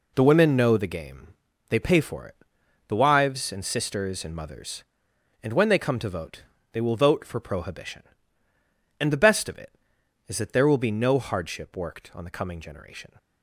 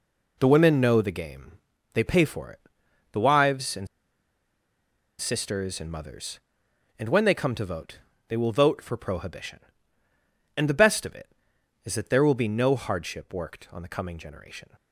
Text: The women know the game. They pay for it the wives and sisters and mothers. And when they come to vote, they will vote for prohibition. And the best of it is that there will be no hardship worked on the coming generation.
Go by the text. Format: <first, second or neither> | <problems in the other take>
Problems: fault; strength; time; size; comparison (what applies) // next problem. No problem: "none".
first | pauses between "it" and "the"; noticeable; at 2.5 s; 0.54 s long; noticeable in the first // pauses between "and" and "sisters"; strong; at 3.8 s; 1.3 s long